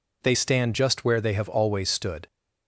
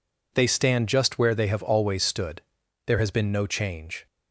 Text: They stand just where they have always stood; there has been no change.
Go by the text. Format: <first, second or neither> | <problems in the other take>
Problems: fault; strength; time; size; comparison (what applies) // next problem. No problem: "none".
second | stops before "there has been no change"; at 2.2 s